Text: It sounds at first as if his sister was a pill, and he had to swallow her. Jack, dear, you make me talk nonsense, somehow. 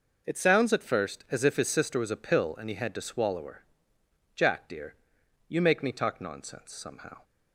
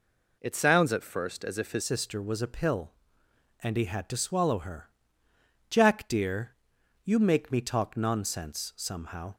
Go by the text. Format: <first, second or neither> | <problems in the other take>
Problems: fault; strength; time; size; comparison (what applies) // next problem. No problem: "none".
first | changes voice at "sister"; from 1.8 s on; 7.5 s long